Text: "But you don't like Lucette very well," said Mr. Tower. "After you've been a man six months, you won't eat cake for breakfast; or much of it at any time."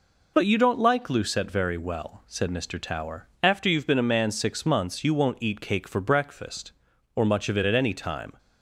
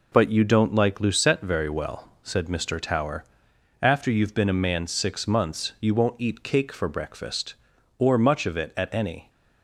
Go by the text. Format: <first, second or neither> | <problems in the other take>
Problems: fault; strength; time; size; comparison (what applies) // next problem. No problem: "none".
first | stops before "time"; at 9.2 s